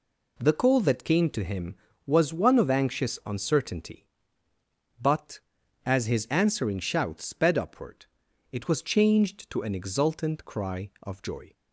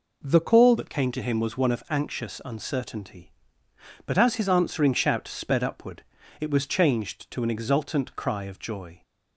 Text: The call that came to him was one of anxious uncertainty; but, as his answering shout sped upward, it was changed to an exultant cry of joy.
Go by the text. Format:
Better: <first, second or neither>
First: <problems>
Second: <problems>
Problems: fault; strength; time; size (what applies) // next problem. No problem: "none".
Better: first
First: none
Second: changes voice at "that"; from 0.7 s on; 8.3 s long